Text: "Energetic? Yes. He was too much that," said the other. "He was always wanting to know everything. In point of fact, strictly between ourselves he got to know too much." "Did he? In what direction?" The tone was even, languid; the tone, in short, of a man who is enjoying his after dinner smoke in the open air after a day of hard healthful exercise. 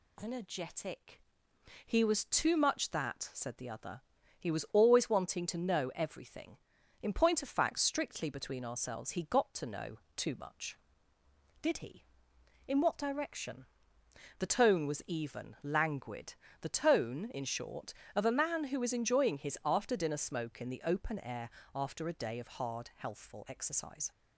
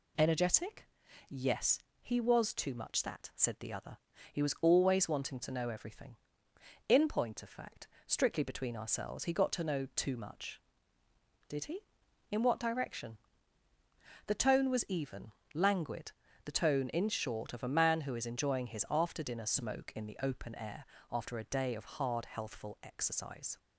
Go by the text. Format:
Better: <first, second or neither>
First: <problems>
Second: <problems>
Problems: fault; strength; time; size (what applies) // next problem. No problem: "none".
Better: second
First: skips "Yes"; at 1.5 s // pauses between "know" and "too"; slight; at 9.9 s; 0.18 s long // pauses between "air" and "after"; slight; at 21.4 s; 0.26 s long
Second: pauses between "air" and "after"; slight; at 20.8 s; 0.26 s long